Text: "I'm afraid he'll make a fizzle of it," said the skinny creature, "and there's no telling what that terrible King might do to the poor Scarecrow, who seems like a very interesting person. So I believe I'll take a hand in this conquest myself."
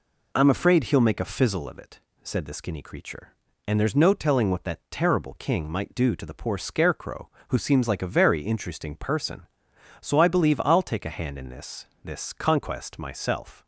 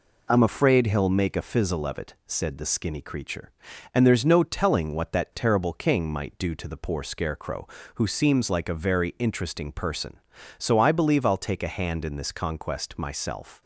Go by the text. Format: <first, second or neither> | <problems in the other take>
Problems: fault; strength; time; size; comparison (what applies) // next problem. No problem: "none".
second | says "this" twice; at 12.0 s